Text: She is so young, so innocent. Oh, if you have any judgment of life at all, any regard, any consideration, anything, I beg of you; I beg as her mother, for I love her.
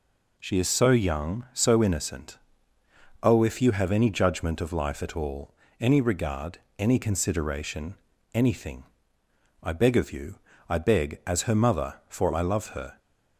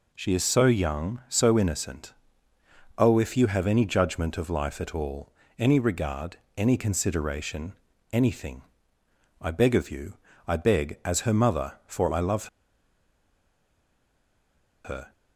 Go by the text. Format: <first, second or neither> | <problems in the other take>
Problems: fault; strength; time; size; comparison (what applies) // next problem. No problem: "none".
first | pauses between "love" and "her"; strong; at 12.4 s; 2.3 s long